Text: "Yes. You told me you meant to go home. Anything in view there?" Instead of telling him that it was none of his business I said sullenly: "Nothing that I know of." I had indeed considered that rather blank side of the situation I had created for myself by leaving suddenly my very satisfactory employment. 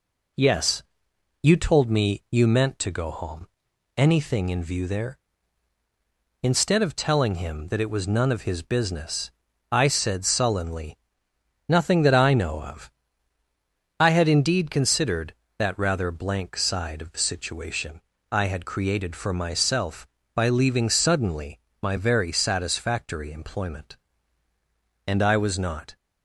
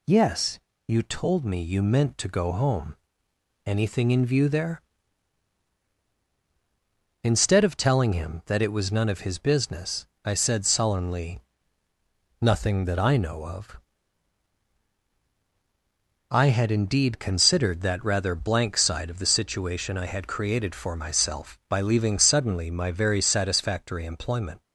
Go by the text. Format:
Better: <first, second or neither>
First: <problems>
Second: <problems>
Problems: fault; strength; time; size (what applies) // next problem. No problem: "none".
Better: second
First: pauses between "business" and "I"; at 9.3 s; 0.40 s long // pauses between "situation" and "I"; slight; at 18.0 s; 0.30 s long // pauses between "suddenly" and "my"; slight; at 21.5 s; 0.24 s long // goes on to say "And I was not"; noticeable; from 25.0 s on; 0.90 s long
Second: pauses between "business" and "I"; slight; at 10.0 s; 0.18 s long